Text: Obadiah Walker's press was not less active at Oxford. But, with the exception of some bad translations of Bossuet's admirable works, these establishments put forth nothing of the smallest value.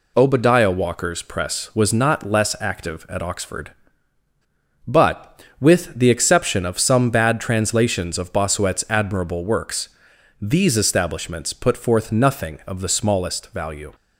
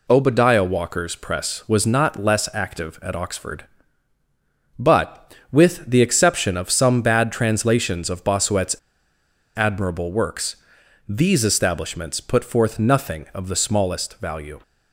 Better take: first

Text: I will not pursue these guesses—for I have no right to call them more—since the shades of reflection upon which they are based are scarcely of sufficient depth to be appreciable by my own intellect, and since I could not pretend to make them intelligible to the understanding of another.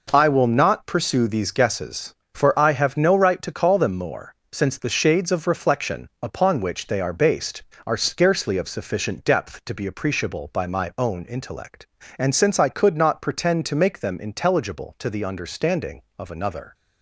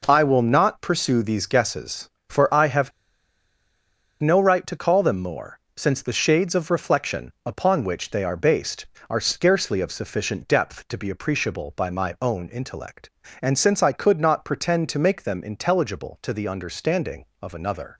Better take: first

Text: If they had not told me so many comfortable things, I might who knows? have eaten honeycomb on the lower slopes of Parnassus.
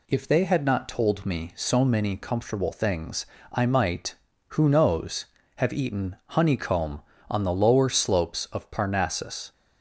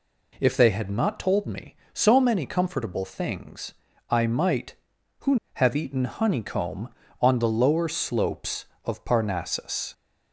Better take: first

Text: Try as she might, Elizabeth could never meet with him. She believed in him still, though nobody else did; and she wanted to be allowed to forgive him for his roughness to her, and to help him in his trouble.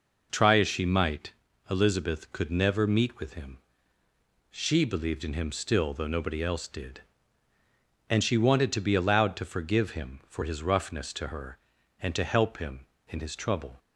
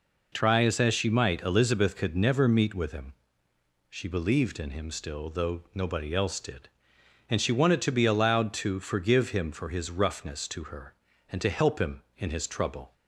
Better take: first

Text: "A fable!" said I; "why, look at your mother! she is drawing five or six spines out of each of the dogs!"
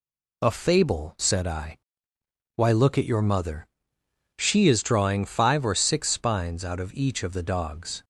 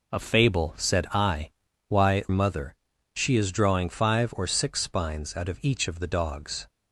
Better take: first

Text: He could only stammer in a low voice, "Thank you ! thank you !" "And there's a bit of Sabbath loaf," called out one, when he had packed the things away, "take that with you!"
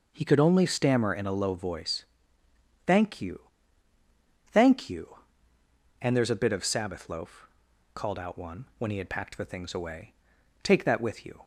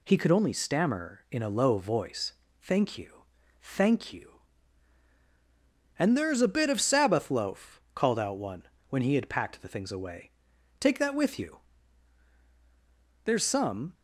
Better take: first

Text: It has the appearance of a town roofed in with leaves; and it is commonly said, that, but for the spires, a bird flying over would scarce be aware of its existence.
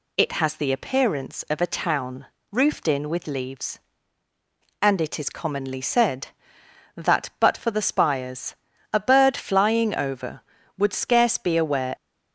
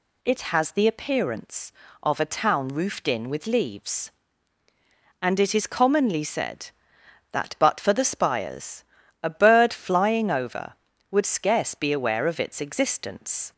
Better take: second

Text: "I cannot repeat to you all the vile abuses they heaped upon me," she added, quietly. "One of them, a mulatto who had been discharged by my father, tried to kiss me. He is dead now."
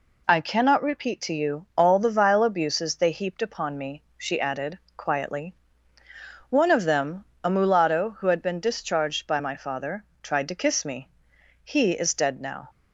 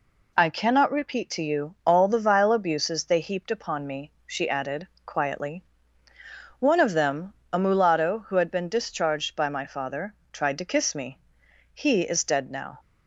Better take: neither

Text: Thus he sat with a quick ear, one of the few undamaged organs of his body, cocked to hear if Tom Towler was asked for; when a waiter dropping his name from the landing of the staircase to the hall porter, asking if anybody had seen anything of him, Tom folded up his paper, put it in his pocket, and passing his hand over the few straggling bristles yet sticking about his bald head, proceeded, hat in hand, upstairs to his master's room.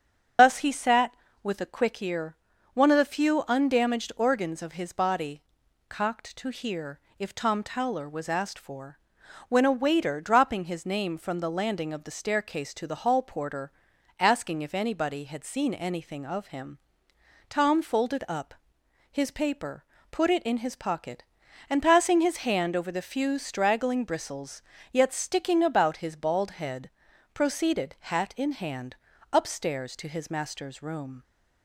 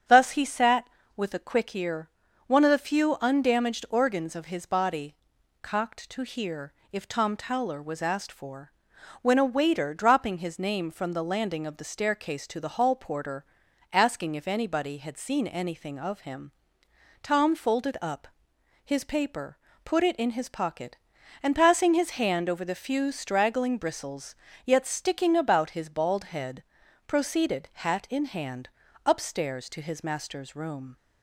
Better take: second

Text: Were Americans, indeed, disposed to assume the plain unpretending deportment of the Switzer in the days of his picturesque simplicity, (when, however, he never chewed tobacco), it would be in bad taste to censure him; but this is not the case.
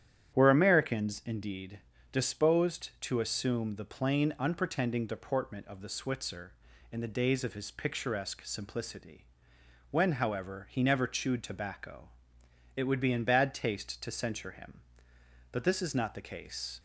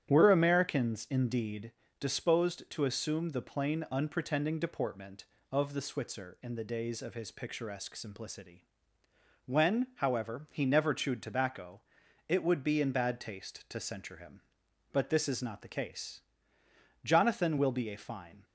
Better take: first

